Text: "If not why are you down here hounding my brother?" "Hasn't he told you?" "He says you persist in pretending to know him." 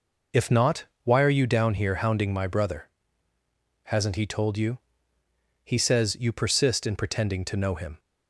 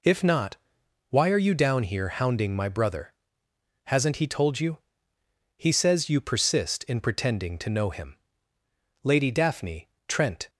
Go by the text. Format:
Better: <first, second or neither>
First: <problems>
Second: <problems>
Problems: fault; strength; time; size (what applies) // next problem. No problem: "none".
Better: first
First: pauses between "not" and "why"; slight; at 0.8 s; 0.18 s long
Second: pauses between "not" and "why"; noticeable; at 0.5 s; 0.54 s long // goes on to say "Lady Daphne Trent"; from 9.0 s on; 1.4 s long